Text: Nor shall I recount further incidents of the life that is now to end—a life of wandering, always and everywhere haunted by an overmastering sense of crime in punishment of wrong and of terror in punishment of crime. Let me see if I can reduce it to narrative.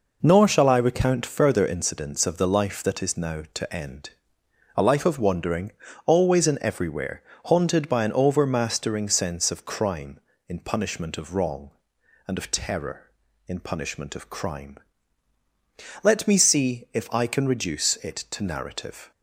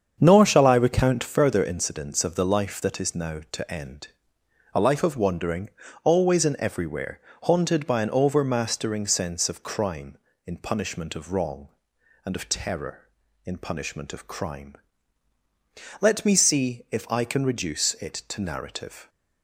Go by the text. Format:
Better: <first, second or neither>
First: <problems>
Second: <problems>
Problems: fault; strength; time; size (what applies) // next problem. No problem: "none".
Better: first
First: pauses between "everywhere" and "haunted"; slight; at 7.2 s; 0.22 s long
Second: starts louder than the rest; strong; until 1.5 s; 7 dB // pauses between "everywhere" and "haunted"; slight; at 7.2 s; 0.22 s long